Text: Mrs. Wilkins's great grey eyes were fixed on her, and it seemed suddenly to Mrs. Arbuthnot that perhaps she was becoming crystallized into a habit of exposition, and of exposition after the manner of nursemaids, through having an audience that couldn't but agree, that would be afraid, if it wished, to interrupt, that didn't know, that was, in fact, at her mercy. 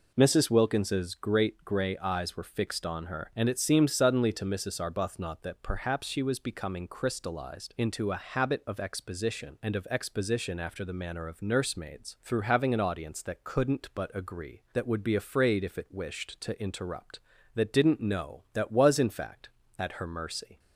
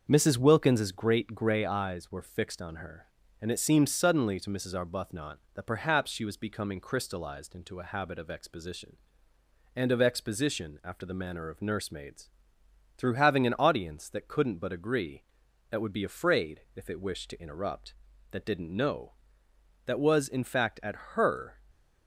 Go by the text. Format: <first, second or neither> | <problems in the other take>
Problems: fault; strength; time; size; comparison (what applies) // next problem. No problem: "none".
first | starts louder than the rest; until 1.1 s; 6.5 dB // pauses between "at" and "her"; slight; at 20.9 s; 0.20 s long // stops before "mercy"; at 21.7 s